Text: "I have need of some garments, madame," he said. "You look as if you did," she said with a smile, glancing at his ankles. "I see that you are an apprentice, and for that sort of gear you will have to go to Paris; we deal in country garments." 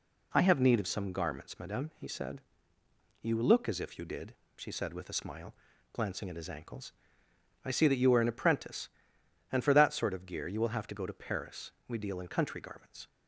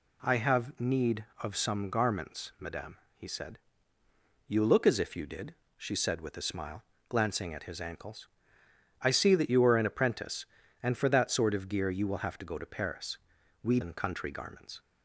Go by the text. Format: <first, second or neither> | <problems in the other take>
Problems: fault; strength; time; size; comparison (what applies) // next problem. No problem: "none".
first | skips "deal"; at 13.7 s